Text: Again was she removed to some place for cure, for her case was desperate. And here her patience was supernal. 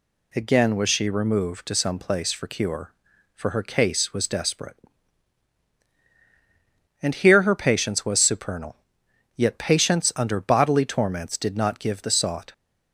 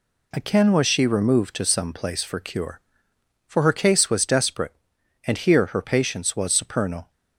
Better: second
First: goes on to say "Yet patience under bodily torments did not give the sought"; strong; from 9.3 s on; 3.1 s long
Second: none

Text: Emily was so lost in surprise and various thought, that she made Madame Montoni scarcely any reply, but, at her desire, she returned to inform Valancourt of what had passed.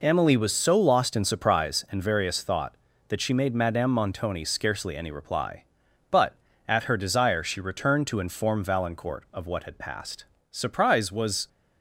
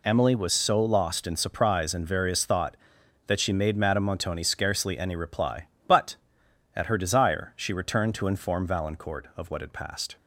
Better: second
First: goes on to say "Surprise was"; noticeable; from 10.4 s on; 0.98 s long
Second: none

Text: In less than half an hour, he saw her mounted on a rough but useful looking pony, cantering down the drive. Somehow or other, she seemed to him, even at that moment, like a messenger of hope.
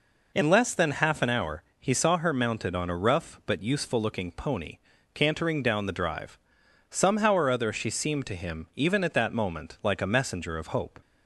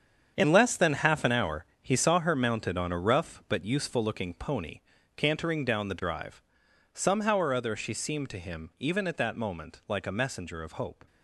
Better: first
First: none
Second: gets quieter; strong; throughout; 10.5 dB

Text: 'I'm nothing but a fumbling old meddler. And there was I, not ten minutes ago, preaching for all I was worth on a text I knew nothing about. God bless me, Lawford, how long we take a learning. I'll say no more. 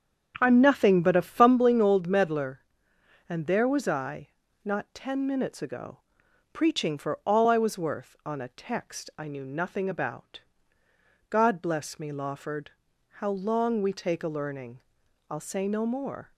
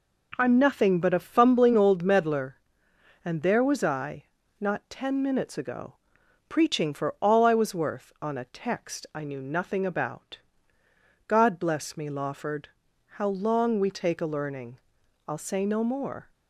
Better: second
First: starts louder than the rest; strong; until 1.6 s; 8 dB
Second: none

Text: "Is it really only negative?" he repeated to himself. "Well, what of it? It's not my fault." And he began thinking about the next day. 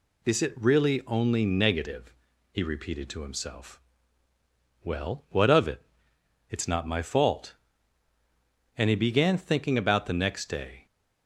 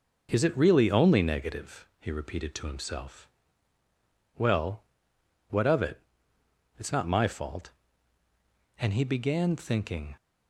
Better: first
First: none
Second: stops before "about the next day"; at 10.1 s

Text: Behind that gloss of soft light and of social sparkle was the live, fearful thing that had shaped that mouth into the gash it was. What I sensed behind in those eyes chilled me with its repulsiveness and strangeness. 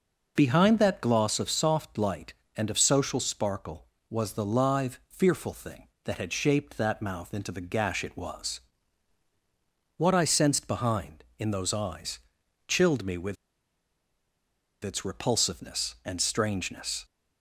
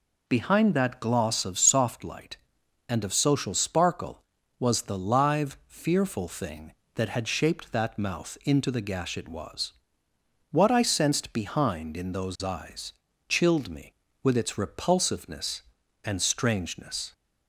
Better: second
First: pauses between "eyes" and "chilled"; noticeable; at 12.1 s; 0.50 s long // pauses between "with" and "its"; strong; at 13.3 s; 1.4 s long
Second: pauses between "eyes" and "chilled"; slight; at 12.9 s; 0.36 s long

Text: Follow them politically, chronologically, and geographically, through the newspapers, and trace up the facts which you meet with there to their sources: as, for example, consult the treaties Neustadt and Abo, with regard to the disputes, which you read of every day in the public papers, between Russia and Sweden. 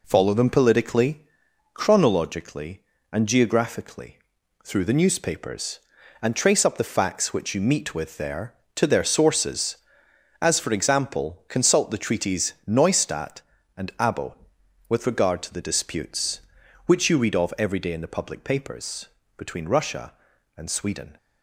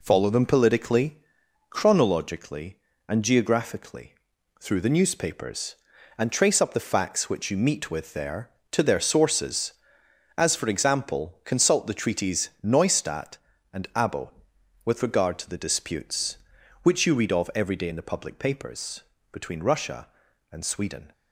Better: neither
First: none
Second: none

